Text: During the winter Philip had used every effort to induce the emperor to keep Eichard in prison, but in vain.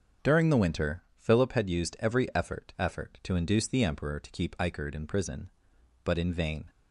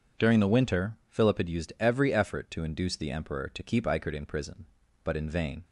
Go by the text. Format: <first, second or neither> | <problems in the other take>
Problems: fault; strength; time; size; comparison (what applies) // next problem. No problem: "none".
second | starts louder than the rest; until 1.3 s; 7 dB // says "effort" twice; at 2.7 s